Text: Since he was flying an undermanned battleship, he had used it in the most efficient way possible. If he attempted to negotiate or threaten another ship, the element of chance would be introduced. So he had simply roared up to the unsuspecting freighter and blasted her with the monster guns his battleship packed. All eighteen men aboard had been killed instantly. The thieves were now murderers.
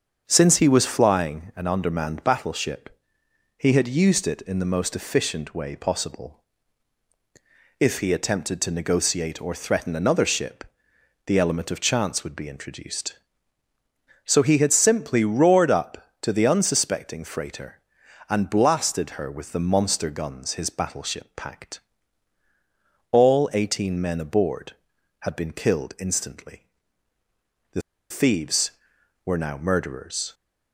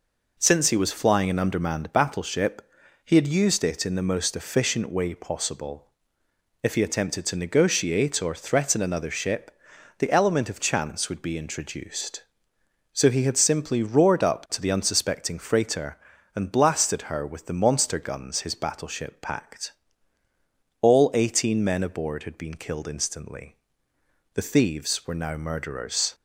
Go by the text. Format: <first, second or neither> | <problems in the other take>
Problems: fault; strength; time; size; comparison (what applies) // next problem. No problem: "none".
second | starts louder than the rest; until 1.2 s; 7 dB // pauses between "The" and "thieves"; slight; at 27.8 s; 0.29 s long